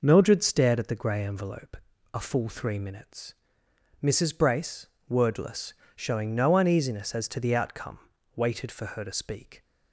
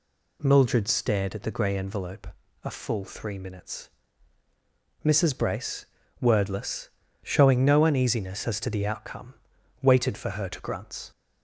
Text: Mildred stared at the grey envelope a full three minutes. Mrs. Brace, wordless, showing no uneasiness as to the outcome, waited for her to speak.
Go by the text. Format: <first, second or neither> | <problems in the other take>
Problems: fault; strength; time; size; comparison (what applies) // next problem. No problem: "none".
first | pauses between "envelope" and "a"; at 2.2 s; 0.38 s long; slight in the first // says "grunts" for "speak"; at 10.6 s